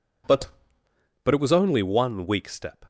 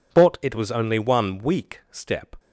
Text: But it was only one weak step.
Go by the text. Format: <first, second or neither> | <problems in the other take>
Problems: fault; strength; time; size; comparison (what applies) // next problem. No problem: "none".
second | says "But" twice; at 1.2 s